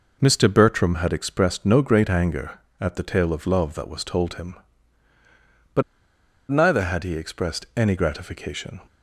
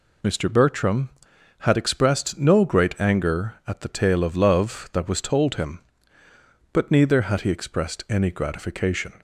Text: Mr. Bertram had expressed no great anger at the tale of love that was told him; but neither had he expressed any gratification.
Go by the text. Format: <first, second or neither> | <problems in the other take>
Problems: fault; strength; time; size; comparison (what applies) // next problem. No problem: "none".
second | pauses between "but" and "neither"; noticeable; at 5.8 s; 0.68 s long